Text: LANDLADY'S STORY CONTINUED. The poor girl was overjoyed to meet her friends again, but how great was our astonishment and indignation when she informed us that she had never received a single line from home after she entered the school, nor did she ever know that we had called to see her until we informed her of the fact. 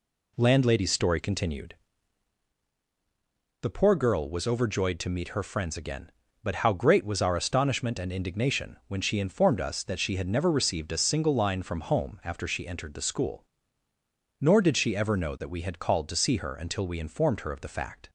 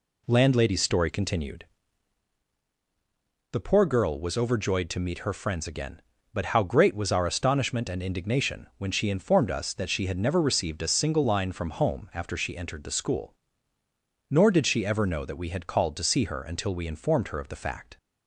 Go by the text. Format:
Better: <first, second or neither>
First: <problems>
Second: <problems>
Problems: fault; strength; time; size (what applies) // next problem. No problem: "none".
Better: neither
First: none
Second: none